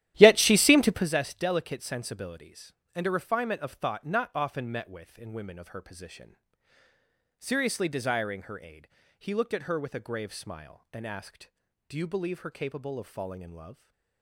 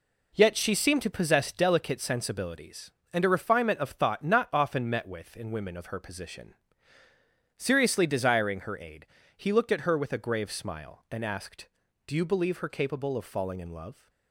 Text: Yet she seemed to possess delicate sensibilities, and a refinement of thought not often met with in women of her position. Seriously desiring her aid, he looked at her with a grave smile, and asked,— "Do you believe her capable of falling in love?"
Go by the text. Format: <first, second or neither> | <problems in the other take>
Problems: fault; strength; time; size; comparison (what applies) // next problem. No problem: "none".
second | starts louder than the rest; strong; until 1.1 s; 13 dB